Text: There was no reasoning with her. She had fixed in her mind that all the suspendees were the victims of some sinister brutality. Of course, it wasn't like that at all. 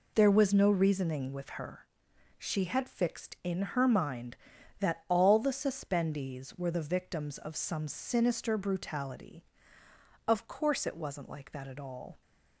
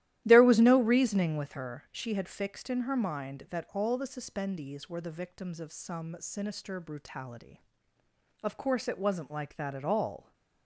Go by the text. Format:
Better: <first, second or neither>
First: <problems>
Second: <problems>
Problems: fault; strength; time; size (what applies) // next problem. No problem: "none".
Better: first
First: none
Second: starts louder than the rest; strong; until 1.5 s; 13.5 dB